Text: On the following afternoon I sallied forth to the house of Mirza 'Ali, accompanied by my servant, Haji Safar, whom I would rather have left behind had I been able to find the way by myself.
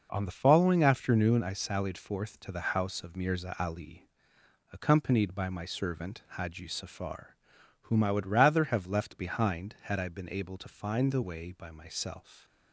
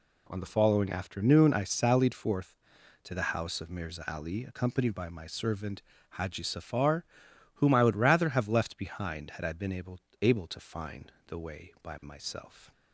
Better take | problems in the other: first | says "able" twice; at 10.2 s // pauses between "find" and "the"; slight; at 11.1 s; 0.16 s long

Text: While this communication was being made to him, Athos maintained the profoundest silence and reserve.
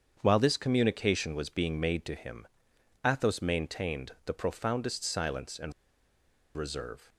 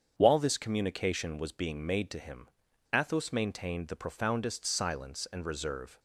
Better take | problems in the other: second | starts louder than the rest; strong; until 1.2 s; 7.5 dB; strong in the second // pauses between "and" and "reserve"; noticeable; at 5.7 s; 0.82 s long

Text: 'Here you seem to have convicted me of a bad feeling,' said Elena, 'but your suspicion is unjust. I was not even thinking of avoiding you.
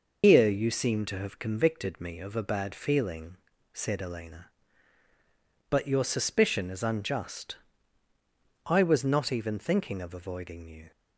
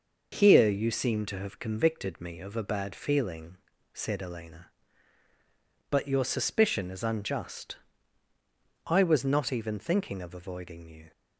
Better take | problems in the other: second | loses the start of "Here"; at 0.2 s; 120 ms

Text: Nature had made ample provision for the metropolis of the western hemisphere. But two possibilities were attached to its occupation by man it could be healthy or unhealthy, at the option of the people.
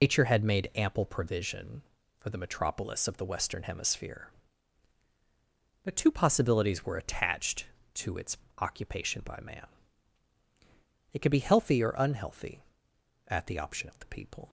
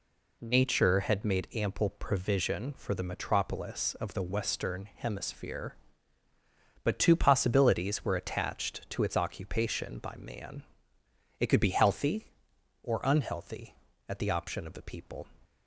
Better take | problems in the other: second | loses the start of "Nature"; at 0.0 s; 145 ms // pauses between "its" and "occupation"; slight; at 8.3 s; 0.22 s long // pauses between "man" and "it"; strong; at 9.6 s; 1.4 s long; noticeable in the second

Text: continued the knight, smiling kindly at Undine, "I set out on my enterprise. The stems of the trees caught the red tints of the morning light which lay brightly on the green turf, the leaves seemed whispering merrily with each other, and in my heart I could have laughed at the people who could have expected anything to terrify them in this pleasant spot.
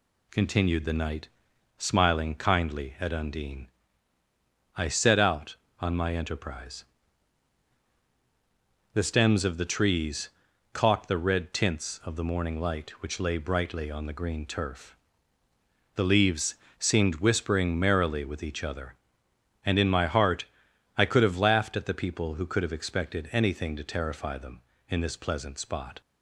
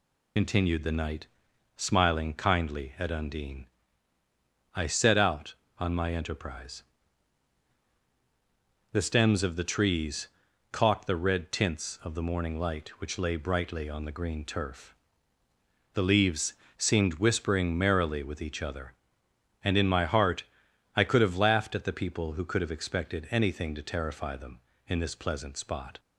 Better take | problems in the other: first | loses the start of "continued"; at 0.3 s; 70 ms // pauses between "trees" and "caught"; at 10.2 s; 0.42 s long; also in the first // pauses between "leaves" and "seemed"; slight; at 16.5 s; 0.22 s long; slight in the first // pauses between "heart" and "I"; noticeable; at 20.4 s; 0.50 s long; noticeable in the first

